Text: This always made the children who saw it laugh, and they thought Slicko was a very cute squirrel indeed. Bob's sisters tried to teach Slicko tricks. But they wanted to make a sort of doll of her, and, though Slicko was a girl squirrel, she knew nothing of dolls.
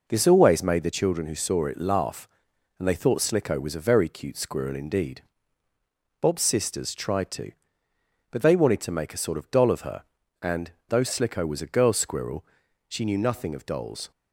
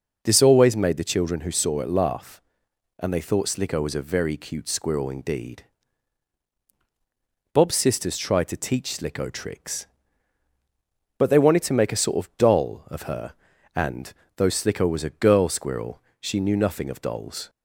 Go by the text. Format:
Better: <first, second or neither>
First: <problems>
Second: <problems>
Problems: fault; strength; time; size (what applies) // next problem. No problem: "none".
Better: second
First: skips "teach Slicko tricks"; at 7.9 s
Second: none